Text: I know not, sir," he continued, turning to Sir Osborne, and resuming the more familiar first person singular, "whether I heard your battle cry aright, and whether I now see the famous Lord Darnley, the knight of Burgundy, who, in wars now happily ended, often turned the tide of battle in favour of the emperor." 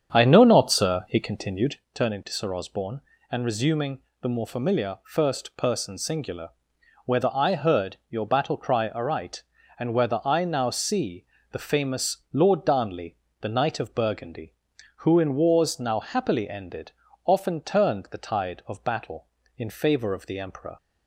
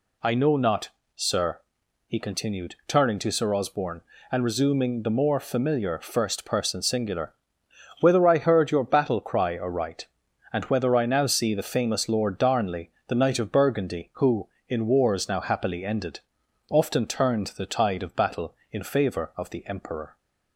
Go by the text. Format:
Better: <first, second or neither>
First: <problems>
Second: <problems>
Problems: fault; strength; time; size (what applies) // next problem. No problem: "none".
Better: second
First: starts louder than the rest; strong; until 1.9 s; 8 dB // pauses between "resuming" and "the"; slight; at 4.0 s; 0.20 s long // pauses between "see" and "the"; slight; at 11.2 s; 0.26 s long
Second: none